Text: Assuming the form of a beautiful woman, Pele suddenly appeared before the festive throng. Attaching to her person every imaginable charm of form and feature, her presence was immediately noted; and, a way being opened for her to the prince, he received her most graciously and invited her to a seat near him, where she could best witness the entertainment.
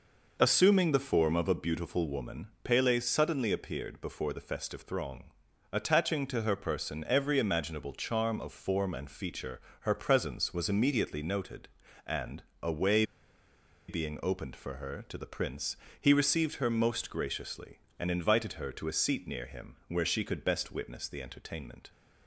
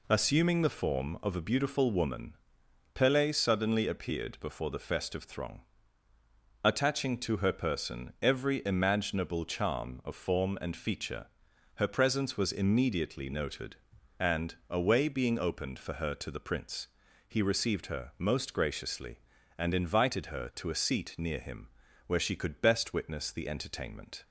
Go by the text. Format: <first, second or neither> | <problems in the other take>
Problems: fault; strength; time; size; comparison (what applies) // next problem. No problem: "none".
second | pauses between "way" and "being"; noticeable; at 13.0 s; 0.84 s long